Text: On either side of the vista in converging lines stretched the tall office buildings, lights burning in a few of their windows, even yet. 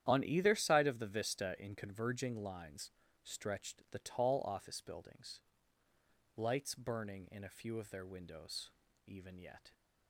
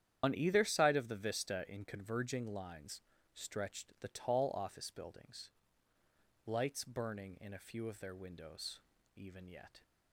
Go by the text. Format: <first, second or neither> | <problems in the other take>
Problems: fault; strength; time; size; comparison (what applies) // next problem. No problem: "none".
first | loses the start of "On"; at 0.2 s; 65 ms // starts louder than the rest; strong; until 1.2 s; 10 dB; strong in the first // pauses between "lines" and "stretched"; slight; at 3.0 s; 0.32 s long; slight in the first